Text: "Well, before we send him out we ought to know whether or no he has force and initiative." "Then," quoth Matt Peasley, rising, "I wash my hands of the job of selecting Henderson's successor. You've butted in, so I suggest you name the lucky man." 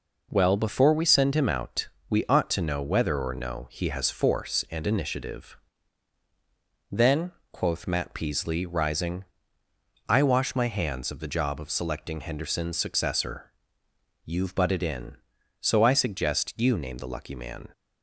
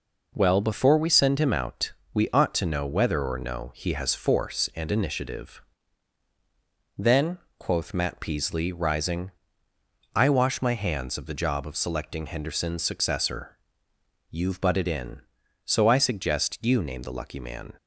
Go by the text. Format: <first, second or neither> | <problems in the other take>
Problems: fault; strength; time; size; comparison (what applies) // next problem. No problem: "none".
neither | pauses between "out" and "we"; slight; the same in both